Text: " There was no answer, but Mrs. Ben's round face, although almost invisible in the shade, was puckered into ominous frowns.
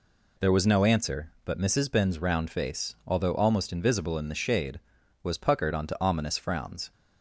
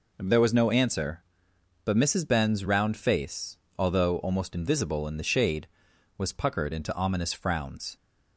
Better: second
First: says "onto" for "into"; at 5.7 s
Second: none

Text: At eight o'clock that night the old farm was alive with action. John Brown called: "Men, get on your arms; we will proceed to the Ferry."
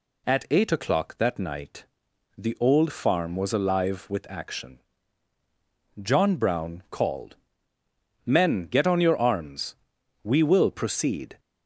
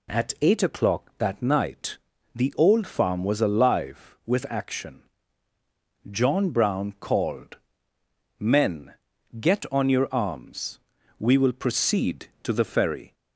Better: second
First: pauses between "night" and "the"; noticeable; at 1.8 s; 0.52 s long // stops before "to the Ferry"; at 11.3 s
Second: pauses between "night" and "the"; slight; at 1.9 s; 0.36 s long

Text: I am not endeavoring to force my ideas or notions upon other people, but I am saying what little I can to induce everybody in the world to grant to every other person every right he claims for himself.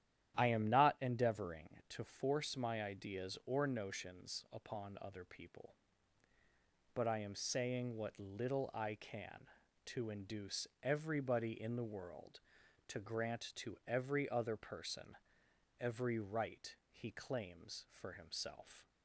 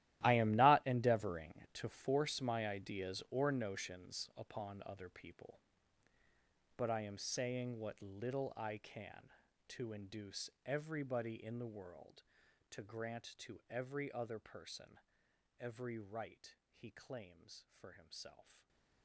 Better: first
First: starts louder than the rest; strong; until 1.4 s; 11.5 dB // pauses between "induce" and "everybody"; slight; at 10.6 s; 0.16 s long // pauses between "person" and "every"; noticeable; at 15.1 s; 0.65 s long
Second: gets quieter; strong; throughout; 17 dB // starts louder than the rest; strong; until 1.2 s; 15 dB // pauses between "induce" and "everybody"; slight; at 10.5 s; 0.16 s long // pauses between "person" and "every"; noticeable; at 14.9 s; 0.62 s long // stays silent after the last word; slight; from 18.5 s on; 0.5 s long

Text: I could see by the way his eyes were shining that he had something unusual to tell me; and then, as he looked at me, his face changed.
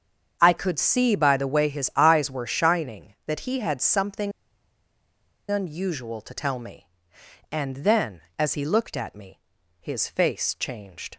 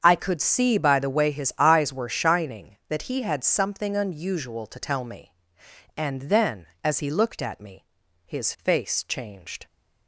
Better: second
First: starts louder than the rest; strong; until 1.4 s; 7.5 dB // pauses between "something" and "unusual"; at 4.3 s; 1.1 s long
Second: starts louder than the rest; strong; until 1.0 s; 7.5 dB

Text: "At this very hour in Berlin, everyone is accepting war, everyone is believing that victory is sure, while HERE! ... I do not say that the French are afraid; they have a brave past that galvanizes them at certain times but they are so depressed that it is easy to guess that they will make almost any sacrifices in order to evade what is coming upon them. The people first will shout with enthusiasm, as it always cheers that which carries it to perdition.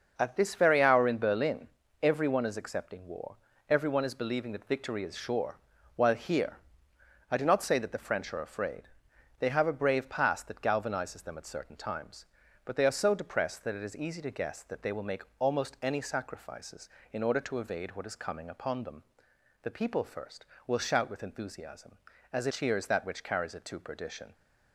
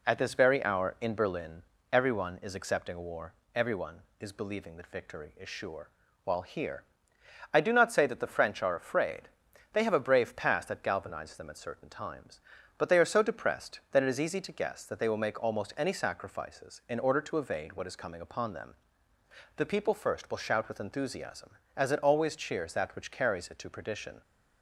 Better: second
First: starts louder than the rest; noticeable; until 1.1 s; 6 dB // pauses between "make" and "almost"; slight; at 15.2 s; 0.16 s long // skips "always"; at 22.5 s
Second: none

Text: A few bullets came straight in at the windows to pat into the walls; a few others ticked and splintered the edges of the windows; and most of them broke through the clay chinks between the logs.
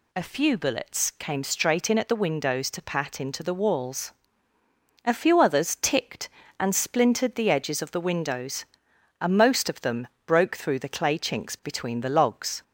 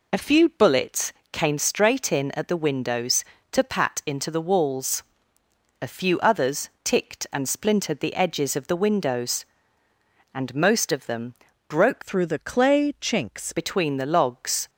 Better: first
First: pauses between "them" and "broke"; slight; at 10.0 s; 0.18 s long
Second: pauses between "bullets" and "came"; slight; at 1.1 s; 0.20 s long // pauses between "others" and "ticked"; slight; at 6.6 s; 0.16 s long // pauses between "them" and "broke"; slight; at 11.3 s; 0.34 s long // changes voice from "through" to "chinks"; from 12.0 to 13.5 s; 1.5 s long

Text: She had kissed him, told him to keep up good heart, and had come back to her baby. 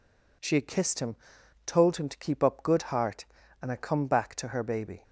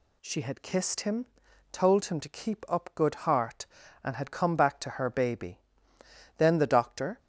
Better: first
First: none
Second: goes on to say "Then the doctor"; noticeable; from 6.3 s on; 0.80 s long

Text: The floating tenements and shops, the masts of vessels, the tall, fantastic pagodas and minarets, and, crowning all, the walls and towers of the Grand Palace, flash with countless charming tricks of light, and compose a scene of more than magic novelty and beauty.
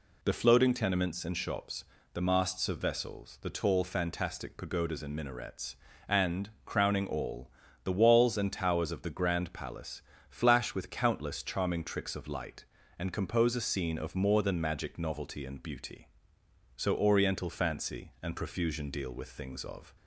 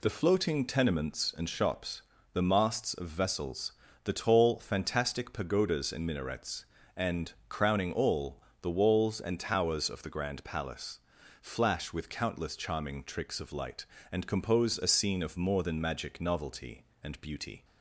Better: second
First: goes on to say "So oriental fancy and profusion deal with things of"; strong; from 16.7 s on; 3.2 s long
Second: none

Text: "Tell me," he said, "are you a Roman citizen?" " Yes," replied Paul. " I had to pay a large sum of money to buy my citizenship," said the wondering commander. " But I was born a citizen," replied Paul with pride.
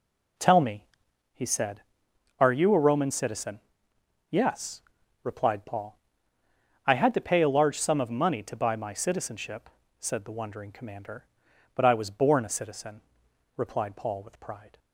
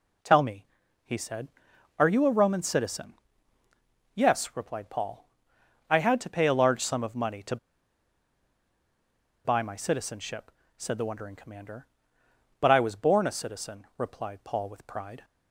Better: first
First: none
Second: pauses between "to" and "buy"; strong; at 7.5 s; 1.8 s long

